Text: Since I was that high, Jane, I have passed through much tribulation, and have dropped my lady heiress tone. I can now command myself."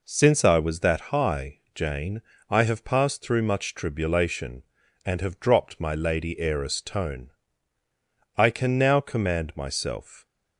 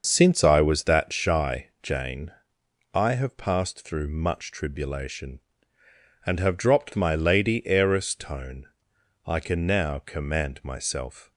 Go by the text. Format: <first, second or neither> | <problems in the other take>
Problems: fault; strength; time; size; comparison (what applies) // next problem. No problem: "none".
first | starts louder than the rest; until 1.0 s; 6.5 dB // says "shy" for "high"; at 1.1 s